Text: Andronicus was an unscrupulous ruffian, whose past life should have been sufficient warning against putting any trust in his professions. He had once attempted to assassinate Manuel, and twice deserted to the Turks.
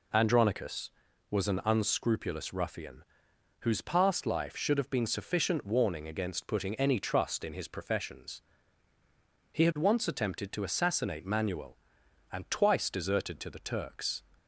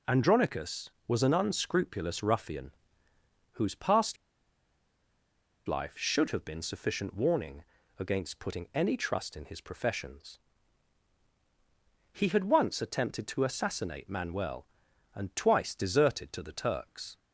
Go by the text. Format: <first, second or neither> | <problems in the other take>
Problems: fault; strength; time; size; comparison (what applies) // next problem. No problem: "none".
first | pauses between "past" and "life"; strong; at 4.1 s; 1.5 s long // pauses between "warning" and "against"; slight; at 7.6 s; 0.34 s long